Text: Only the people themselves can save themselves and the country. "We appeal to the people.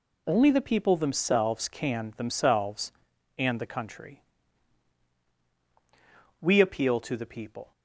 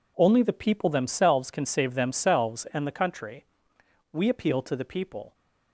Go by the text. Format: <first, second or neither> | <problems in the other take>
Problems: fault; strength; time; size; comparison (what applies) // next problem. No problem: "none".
second | skips "save"; at 2.1 s